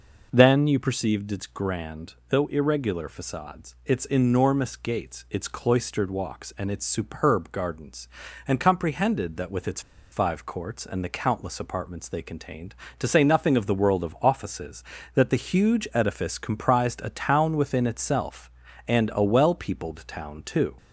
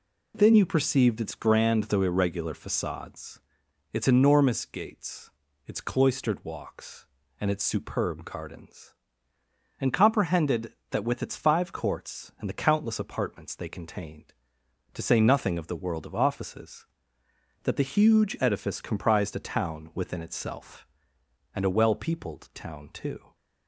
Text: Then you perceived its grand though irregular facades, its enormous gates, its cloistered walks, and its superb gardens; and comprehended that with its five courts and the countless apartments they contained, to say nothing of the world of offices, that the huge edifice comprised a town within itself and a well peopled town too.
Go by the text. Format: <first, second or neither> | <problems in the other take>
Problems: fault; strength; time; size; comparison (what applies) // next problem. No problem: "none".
second | pauses between "its" and "five"; slight; at 9.7 s; 0.31 s long